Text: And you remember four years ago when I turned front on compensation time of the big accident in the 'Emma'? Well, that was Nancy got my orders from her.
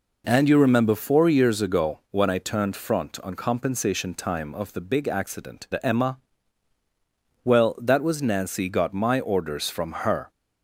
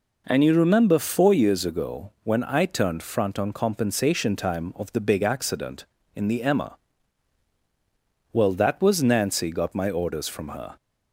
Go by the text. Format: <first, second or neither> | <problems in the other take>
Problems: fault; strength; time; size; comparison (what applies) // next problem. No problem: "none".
second | skips "in"; at 5.6 s